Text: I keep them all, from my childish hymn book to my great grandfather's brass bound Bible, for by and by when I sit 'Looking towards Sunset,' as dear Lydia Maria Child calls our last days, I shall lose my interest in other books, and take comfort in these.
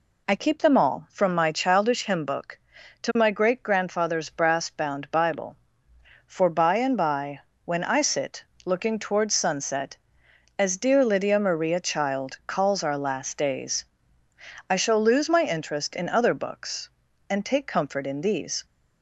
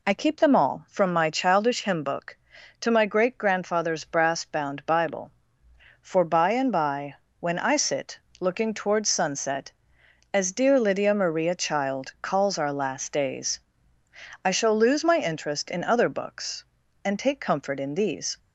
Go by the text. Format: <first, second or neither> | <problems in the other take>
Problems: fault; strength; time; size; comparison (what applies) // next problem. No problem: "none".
neither | pauses between "by" and "when"; slight; the same in both // pauses between "sit" and "Looking"; slight; the same in both